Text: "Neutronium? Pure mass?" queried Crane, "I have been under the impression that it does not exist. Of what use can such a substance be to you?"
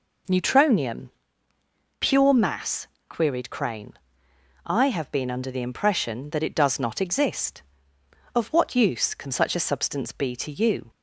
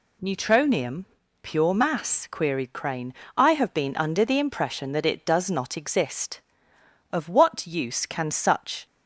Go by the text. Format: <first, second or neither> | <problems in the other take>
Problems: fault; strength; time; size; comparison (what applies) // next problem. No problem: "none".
first | stops before "a substance be to you"; at 8.8 s